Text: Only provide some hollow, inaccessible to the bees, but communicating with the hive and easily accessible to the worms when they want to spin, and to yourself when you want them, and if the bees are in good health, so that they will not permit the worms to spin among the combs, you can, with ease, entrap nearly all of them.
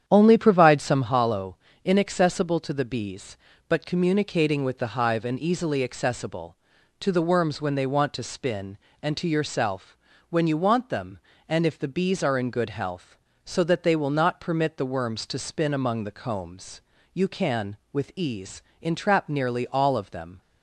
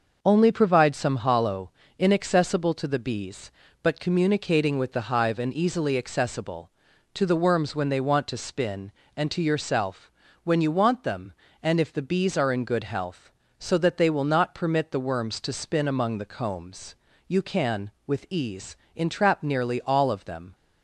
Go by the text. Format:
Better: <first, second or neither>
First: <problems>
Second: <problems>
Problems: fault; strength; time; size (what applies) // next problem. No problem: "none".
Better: second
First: starts louder than the rest; strong; until 1.2 s; 9 dB // pauses between "yourself" and "when"; slight; at 9.9 s; 0.34 s long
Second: pauses between "yourself" and "when"; slight; at 10.1 s; 0.34 s long